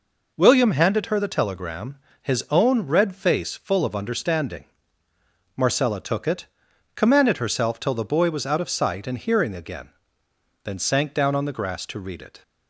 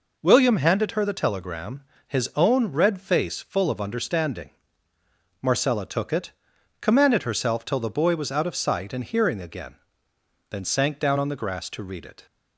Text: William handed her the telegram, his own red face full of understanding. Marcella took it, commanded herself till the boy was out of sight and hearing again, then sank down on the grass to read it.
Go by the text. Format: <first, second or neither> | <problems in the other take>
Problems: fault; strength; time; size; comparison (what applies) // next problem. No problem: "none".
neither | none